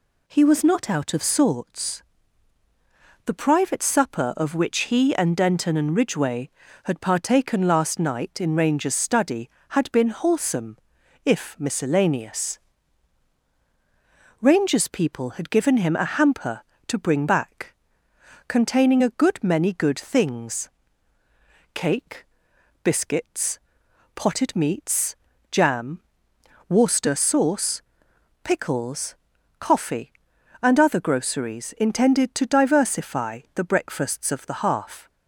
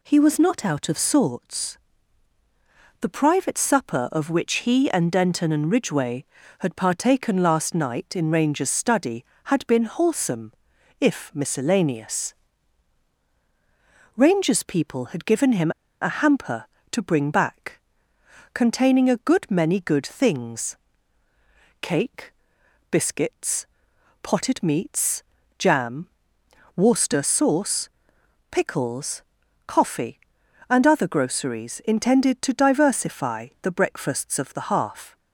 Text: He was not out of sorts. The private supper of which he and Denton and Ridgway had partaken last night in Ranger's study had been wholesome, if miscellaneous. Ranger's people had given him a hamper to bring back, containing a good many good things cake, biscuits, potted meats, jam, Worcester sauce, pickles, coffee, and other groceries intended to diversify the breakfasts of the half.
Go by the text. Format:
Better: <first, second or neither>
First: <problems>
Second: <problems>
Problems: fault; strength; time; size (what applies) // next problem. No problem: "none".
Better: first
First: pauses between "things" and "cake"; at 20.6 s; 1.0 s long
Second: pauses between "him" and "a"; slight; at 15.7 s; 0.29 s long // pauses between "things" and "cake"; at 20.7 s; 1.0 s long